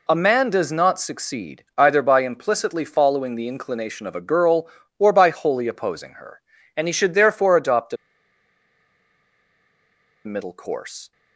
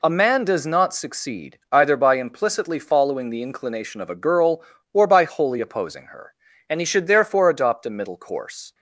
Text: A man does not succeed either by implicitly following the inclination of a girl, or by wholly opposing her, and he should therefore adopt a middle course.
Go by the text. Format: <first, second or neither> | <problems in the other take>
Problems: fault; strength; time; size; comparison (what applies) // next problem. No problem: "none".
second | pauses between "a" and "middle"; strong; at 7.9 s; 2.2 s long